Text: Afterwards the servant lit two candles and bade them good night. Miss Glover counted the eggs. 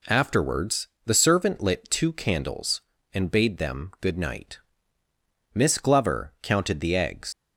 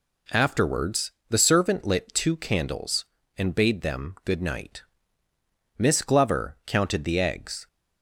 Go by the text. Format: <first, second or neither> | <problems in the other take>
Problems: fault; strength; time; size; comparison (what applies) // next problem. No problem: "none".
second | pauses between "Afterwards" and "the"; slight; at 0.8 s; 0.16 s long; slight in the second // leaves "eggs" unfinished; at 7.3 s; 105 ms